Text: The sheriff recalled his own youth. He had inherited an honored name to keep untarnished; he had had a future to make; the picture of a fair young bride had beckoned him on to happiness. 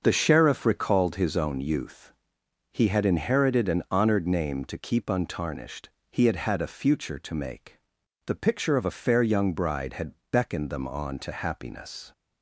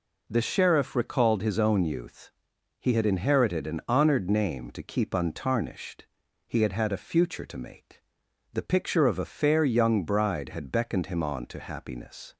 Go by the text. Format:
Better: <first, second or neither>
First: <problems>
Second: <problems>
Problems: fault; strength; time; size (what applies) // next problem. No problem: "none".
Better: second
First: starts louder than the rest; until 1.0 s; 6.5 dB // pauses between "had" and "beckoned"; slight; at 10.1 s; 0.18 s long // says "them" for "him"; at 10.7 s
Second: none